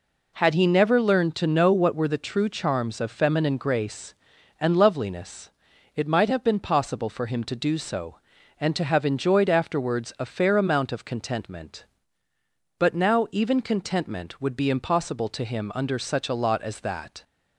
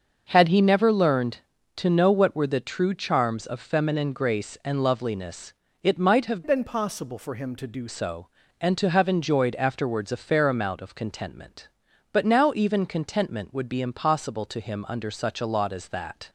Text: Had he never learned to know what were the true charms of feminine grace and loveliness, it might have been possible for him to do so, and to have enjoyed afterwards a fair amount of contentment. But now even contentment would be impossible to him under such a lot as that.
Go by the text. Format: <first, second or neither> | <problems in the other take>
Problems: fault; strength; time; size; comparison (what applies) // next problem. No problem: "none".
first | starts louder than the rest; until 1.2 s; 6 dB // changes voice from "been" to "do"; from 6.4 to 7.8 s; 1.4 s long